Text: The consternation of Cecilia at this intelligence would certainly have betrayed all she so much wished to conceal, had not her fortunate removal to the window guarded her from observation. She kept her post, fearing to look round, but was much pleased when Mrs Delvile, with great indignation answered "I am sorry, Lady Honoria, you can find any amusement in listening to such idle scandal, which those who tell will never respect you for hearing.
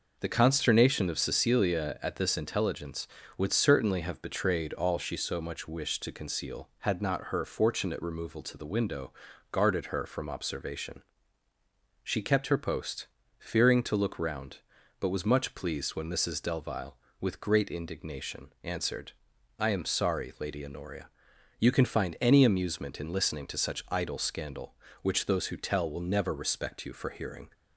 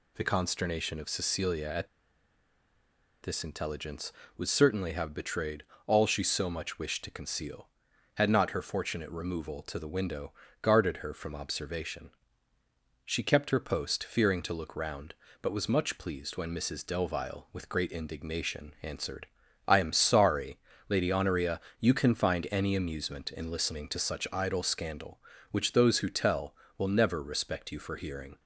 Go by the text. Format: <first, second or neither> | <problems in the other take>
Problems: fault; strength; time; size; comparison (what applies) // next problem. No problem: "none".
first | pauses between "at" and "this"; strong; at 1.8 s; 1.3 s long // pauses between "betrayed" and "all"; slight; at 5.6 s; 0.22 s long // pauses between "window" and "guarded"; slight; at 10.3 s; 0.30 s long; also in the first // pauses between "answered" and "I"; at 19.2 s; 0.40 s long; noticeable in the first